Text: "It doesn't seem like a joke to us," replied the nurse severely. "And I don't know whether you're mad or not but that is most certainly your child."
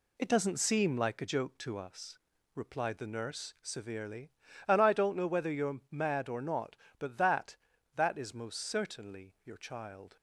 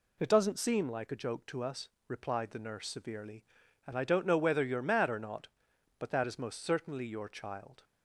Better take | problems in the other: second | says "that" twice; at 7.9 s

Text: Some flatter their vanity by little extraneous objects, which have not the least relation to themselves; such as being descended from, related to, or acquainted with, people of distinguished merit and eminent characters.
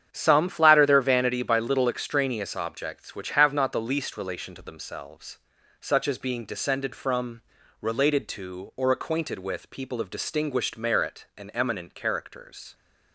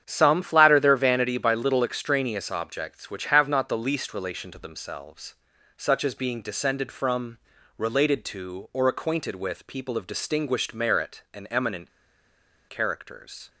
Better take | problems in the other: first | starts louder than the rest; strong; until 1.0 s; 8.5 dB; strong in the first // pauses between "eminent" and "characters"; noticeable; at 11.8 s; 0.79 s long

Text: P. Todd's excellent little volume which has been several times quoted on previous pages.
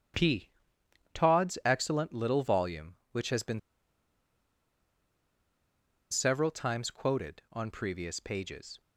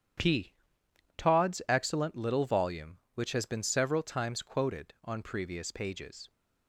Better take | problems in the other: second | starts louder than the rest; strong; until 1.8 s; 9.5 dB; strong in the second // pauses between "been" and "several"; strong; at 3.5 s; 2.5 s long

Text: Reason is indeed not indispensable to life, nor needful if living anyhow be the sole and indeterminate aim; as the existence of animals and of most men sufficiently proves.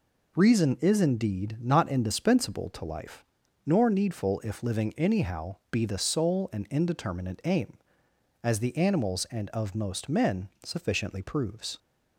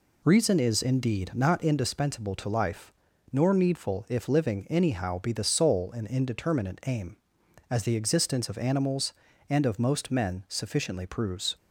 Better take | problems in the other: second | skips "existence of"; at 8.7 s // pauses between "men" and "sufficiently"; slight; at 10.4 s; 0.16 s long

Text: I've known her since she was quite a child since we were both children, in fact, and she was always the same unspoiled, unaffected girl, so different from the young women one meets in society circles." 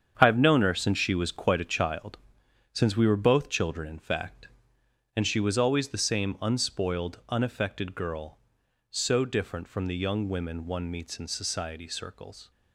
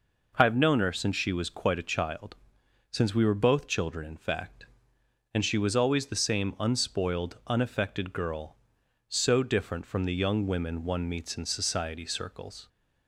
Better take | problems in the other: second | gets quieter; strong; throughout; 9.5 dB // pauses between "child" and "since"; noticeable; at 2.1 s; 0.54 s long; noticeable in the second

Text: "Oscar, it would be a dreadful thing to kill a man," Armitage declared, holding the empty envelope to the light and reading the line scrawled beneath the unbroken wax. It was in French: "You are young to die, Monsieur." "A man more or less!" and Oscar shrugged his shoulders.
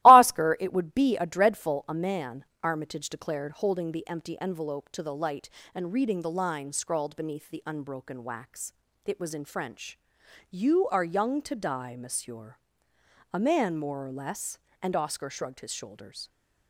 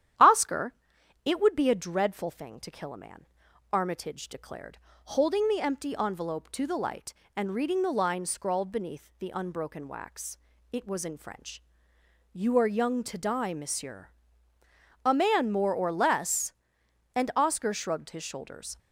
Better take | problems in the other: second | starts louder than the rest; strong; until 1.0 s; 17 dB; strong in the second // skips "thing to kill"; at 1.8 s

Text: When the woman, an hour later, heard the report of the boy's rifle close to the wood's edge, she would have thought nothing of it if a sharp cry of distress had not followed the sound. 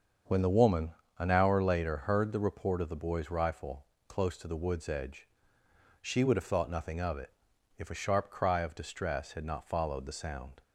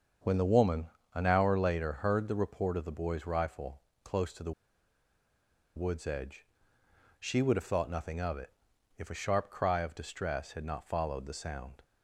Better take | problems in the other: first | starts louder than the rest; until 1.5 s; 7 dB; also in the first // pauses between "rifle" and "close"; slight; at 3.8 s; 0.24 s long; slight in the first // pauses between "the" and "wood's"; at 4.5 s; 1.2 s long // pauses between "it" and "if"; noticeable; at 8.5 s; 0.46 s long; noticeable in the first

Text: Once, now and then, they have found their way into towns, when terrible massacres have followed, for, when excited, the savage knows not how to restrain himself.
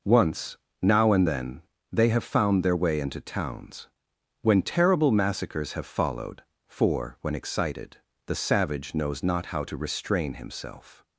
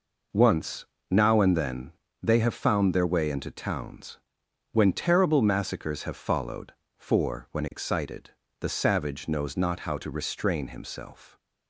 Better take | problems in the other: neither | none

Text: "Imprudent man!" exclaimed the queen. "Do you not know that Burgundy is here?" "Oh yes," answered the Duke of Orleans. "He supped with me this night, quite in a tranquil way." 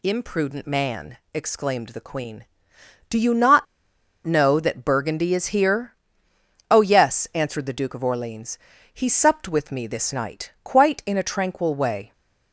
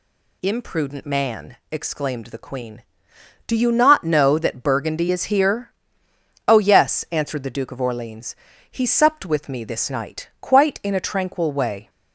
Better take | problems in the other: second | pauses between "not" and "know"; noticeable; at 3.6 s; 0.60 s long

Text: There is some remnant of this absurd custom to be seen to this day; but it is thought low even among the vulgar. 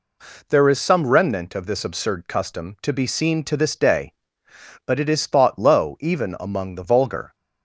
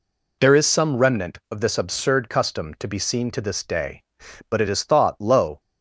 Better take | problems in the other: first | stops before "even among the vulgar"; at 5.5 s

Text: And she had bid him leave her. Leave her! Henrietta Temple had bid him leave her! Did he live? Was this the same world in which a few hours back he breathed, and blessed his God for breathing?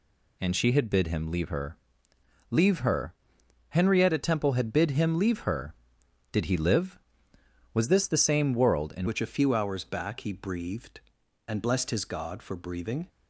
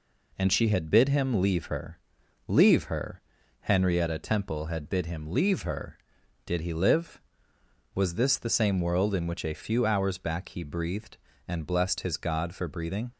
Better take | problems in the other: second | changes voice at "which"; from 9.0 s on; 4.0 s long

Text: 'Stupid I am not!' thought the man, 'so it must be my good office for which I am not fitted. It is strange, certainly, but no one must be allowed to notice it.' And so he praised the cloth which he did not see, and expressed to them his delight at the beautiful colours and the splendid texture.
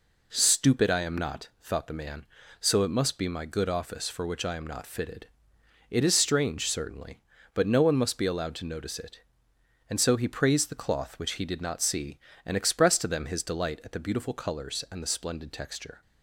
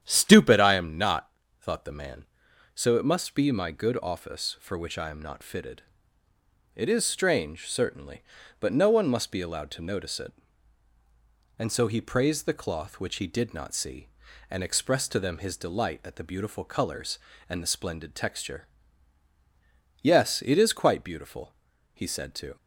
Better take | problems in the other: first | starts louder than the rest; strong; until 1.0 s; 9.5 dB // goes on to say "Yes it is quite beautiful he said to"; strong; from 20.0 s on; 2.5 s long

